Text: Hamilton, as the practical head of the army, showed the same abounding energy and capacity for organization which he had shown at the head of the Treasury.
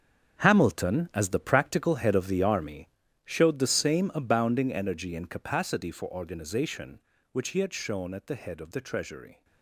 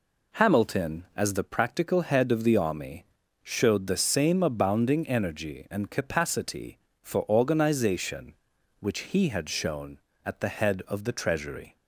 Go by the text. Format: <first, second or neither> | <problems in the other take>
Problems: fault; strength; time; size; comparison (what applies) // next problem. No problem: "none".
second | gets quieter; strong; throughout; 13 dB